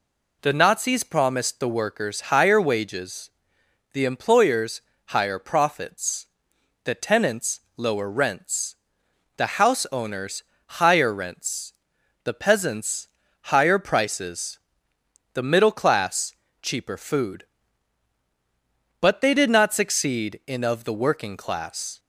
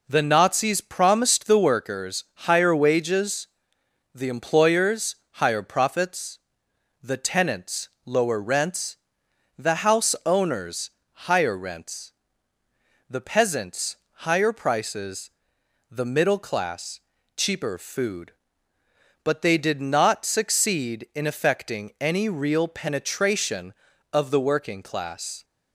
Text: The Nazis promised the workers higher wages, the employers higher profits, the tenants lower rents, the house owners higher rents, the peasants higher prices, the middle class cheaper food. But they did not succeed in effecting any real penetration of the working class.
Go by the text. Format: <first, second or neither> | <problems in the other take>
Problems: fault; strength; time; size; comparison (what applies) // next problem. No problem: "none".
second | pauses between "employers" and "higher"; slight; at 4.8 s; 0.26 s long; slight in the second // pauses between "tenants" and "lower"; slight; at 7.5 s; 0.16 s long; slight in the second // pauses between "owners" and "higher"; slight; at 10.4 s; 0.22 s long; slight in the second // pauses between "peasants" and "higher"; slight; at 13.0 s; 0.36 s long; slight in the second // pauses between "class" and "cheaper"; slight; at 16.3 s; 0.28 s long; also in the second // skips "effecting any real penetration"; at 20.6 s